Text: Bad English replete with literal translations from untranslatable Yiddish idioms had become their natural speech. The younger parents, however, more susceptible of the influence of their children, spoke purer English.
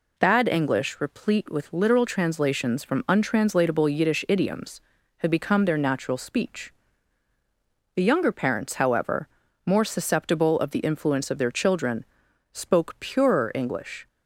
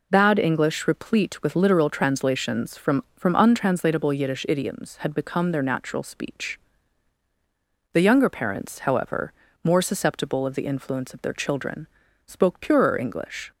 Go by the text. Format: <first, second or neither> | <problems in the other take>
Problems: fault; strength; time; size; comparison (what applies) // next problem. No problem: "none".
first | says "from" twice; at 3.1 s